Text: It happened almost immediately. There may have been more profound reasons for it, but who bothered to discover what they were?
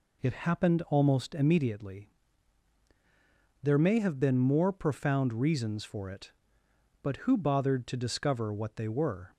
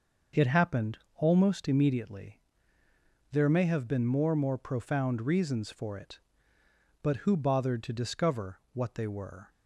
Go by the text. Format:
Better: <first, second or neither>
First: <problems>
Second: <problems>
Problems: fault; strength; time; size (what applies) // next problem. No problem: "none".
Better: first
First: none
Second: starts louder than the rest; noticeable; until 1.5 s; 6 dB // pauses between "happened" and "almost"; slight; at 0.9 s; 0.16 s long // says "more" twice; at 4.3 s